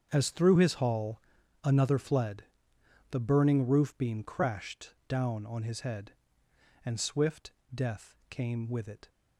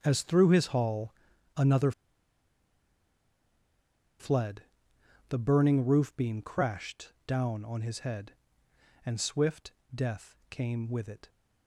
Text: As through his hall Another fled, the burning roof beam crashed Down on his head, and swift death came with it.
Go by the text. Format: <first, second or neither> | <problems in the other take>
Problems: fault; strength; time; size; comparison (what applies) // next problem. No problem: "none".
first | starts louder than the rest; strong; until 1.0 s; 7 dB; strong in the first // pauses between "hall" and "Another"; at 1.1 s; 0.44 s long; also in the first // pauses between "Another" and "fled"; strong; at 1.9 s; 2.2 s long // pauses between "swift" and "death"; slight; at 9.7 s; 0.24 s long; slight in the first // pauses between "death" and "came"; slight; at 10.3 s; 0.16 s long; slight in the first